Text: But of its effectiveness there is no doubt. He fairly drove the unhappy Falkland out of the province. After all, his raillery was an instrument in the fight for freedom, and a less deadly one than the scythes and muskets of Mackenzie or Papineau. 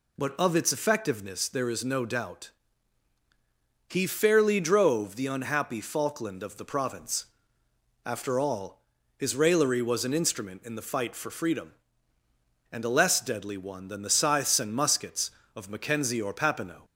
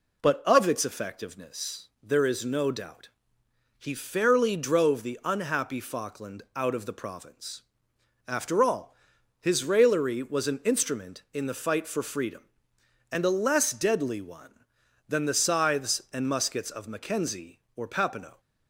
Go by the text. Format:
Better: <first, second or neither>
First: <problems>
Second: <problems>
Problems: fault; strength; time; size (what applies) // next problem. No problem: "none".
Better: second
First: skips "out"; at 6.4 s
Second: none